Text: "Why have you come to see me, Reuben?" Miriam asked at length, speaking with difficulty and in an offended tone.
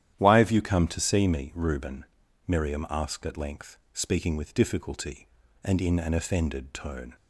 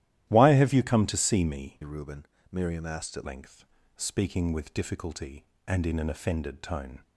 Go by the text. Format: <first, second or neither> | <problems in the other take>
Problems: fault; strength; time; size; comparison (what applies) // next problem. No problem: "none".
first | starts louder than the rest; strong; until 1.3 s; 13 dB; strong in the first // changes voice from "Reuben" to "at"; from 1.8 to 3.2 s; 1.4 s long